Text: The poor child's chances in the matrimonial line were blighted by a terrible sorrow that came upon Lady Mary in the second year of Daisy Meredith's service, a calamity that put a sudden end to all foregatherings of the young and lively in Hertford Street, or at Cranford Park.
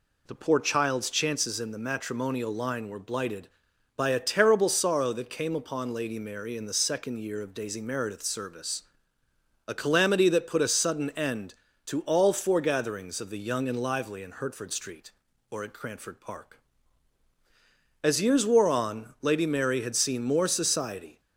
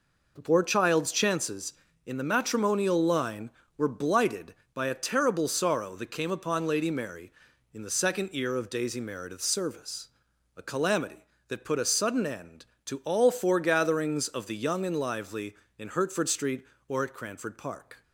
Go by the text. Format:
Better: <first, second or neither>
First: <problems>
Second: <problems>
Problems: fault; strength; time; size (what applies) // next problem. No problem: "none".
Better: second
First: goes on to say "As years wore on Lady Mary had seen more society"; strong; from 18.0 s on; 3.1 s long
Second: none